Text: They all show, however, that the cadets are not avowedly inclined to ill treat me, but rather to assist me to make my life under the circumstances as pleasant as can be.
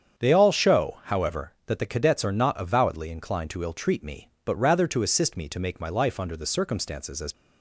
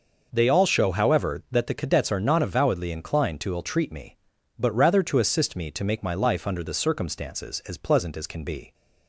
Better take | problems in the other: second | starts louder than the rest; strong; until 1.2 s; 8 dB // stops before "pleasant as can be"; at 7.3 s

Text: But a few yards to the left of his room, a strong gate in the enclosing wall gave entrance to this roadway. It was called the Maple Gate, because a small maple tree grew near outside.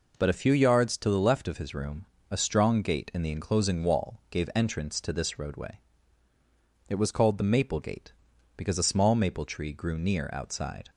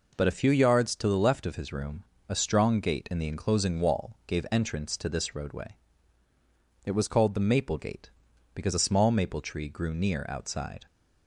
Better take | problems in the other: neither | none

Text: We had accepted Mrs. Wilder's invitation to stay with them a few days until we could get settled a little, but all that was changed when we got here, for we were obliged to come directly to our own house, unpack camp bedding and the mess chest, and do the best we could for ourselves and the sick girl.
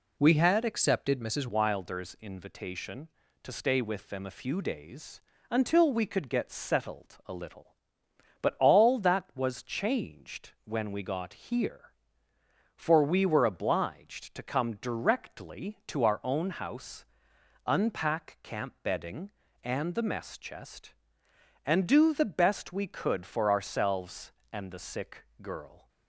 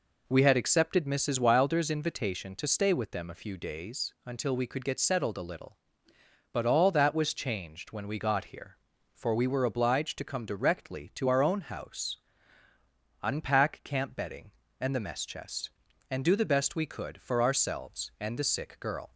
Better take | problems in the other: second | changes voice at "Wilder's"; from 1.4 s on; 24.4 s long // pauses between "days" and "until"; slight; at 5.2 s; 0.30 s long // pauses between "sick" and "girl"; slight; at 25.2 s; 0.16 s long

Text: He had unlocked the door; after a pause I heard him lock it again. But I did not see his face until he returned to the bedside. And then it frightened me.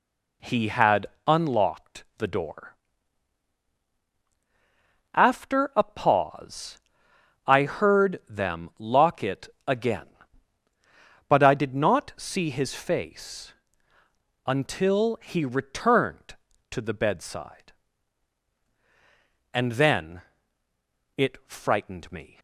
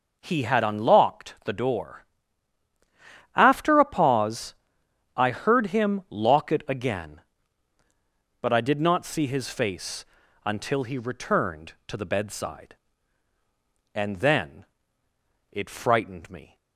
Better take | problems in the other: second | pauses between "had" and "unlocked"; slight; at 1.0 s; 0.22 s long // pauses between "pause" and "I"; noticeable; at 6.7 s; 0.66 s long; noticeable in the second // says "them" for "him"; at 8.2 s // pauses between "it" and "again"; slight; at 9.4 s; 0.18 s long // pauses between "face" and "until"; noticeable; at 13.5 s; 0.94 s long; also in the second // pauses between "then" and "it"; noticeable; at 20.2 s; 0.96 s long; noticeable in the second

